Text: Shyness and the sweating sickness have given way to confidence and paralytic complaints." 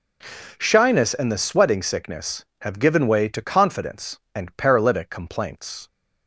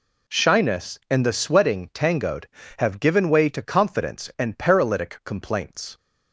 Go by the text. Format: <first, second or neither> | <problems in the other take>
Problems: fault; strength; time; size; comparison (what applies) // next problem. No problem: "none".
first | says "tangoed" for "sickness"; at 1.9 s